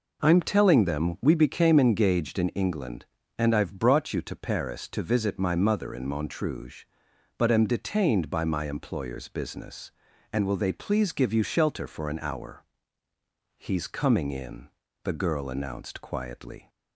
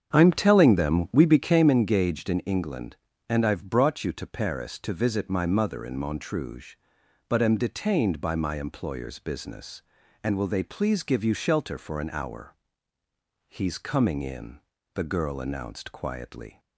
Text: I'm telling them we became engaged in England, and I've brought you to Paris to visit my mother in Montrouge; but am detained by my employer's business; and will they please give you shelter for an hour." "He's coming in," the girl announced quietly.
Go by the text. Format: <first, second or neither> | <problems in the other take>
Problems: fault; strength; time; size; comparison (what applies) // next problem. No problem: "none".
first | starts louder than the rest; strong; until 1.8 s; 8 dB